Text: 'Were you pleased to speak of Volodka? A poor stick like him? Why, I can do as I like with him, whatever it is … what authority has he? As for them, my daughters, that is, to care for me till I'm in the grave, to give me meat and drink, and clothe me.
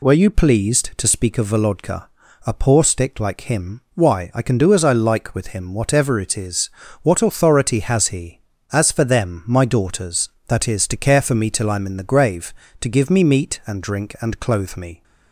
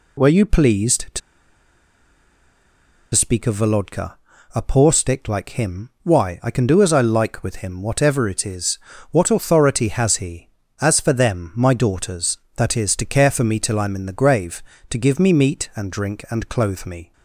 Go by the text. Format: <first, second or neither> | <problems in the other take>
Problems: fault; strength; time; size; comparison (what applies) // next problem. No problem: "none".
first | pauses between "to" and "speak"; strong; at 1.2 s; 1.9 s long